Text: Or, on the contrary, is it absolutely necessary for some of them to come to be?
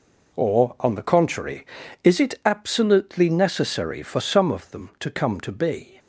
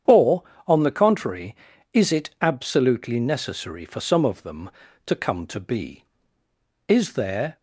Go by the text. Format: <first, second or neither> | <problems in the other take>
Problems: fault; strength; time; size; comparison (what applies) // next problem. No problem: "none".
first | starts louder than the rest; strong; until 1.2 s; 8.5 dB // goes on to say "Is there"; noticeable; from 6.8 s on; 0.68 s long